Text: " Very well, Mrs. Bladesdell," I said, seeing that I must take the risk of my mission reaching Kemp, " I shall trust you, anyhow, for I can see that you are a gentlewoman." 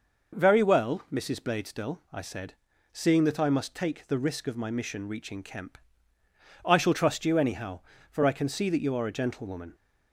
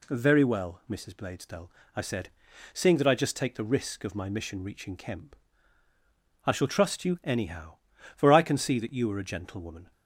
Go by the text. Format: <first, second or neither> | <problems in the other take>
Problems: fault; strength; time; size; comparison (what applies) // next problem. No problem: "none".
first | says "just" for "must"; at 3.1 s